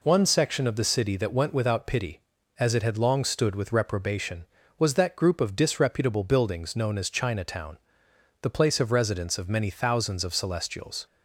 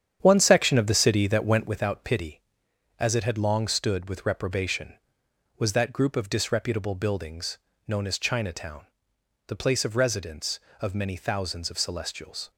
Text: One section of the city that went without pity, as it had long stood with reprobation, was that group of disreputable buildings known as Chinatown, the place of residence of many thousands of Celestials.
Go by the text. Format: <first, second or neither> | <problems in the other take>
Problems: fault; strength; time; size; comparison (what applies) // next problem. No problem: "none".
first | starts louder than the rest; strong; until 1.8 s; 9 dB // pauses between "buildings" and "known"; slight; at 7.5 s; 0.32 s long